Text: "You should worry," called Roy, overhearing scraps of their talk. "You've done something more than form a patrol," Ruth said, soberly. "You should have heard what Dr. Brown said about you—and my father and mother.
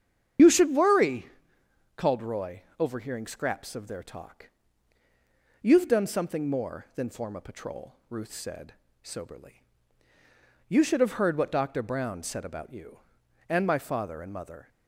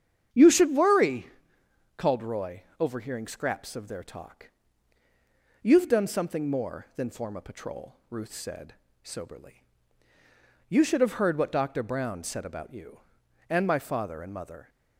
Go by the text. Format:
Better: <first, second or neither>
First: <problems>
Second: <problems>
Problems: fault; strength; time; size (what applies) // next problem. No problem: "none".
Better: second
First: loses the start of "You"; at 0.3 s; 75 ms // starts louder than the rest; strong; until 2.1 s; 8.5 dB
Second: starts louder than the rest; strong; until 2.0 s; 8 dB